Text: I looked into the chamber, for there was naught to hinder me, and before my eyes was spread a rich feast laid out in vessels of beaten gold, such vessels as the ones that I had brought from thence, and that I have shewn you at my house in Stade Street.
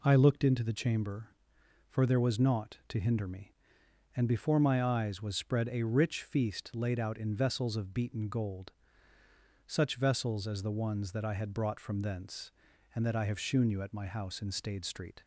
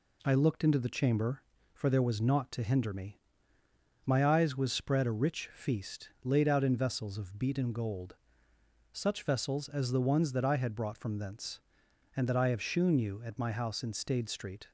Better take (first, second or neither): first